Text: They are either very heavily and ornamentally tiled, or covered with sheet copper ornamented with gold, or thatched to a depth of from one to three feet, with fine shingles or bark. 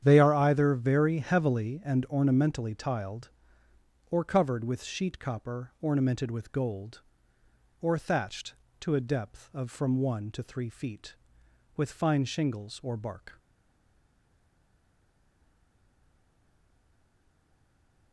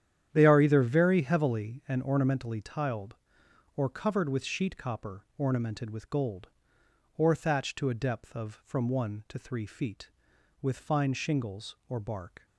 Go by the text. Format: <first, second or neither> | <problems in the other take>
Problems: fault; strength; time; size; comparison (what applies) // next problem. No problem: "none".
second | starts louder than the rest; strong; until 1.0 s; 9 dB; strong in the second // stays silent after the last word; strong; from 13.3 s on; 4.8 s long